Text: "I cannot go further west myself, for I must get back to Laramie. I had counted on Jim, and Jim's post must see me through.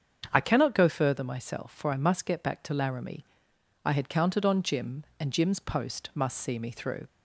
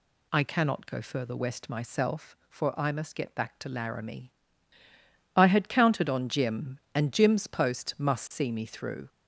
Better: second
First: starts louder than the rest; strong; until 1.3 s; 7.5 dB // skips "west"; at 1.2 s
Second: none

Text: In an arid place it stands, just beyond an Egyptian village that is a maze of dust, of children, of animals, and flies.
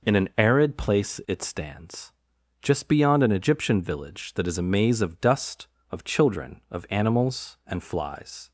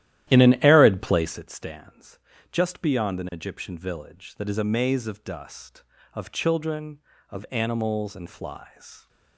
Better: first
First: none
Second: starts louder than the rest; strong; until 1.5 s; 13 dB

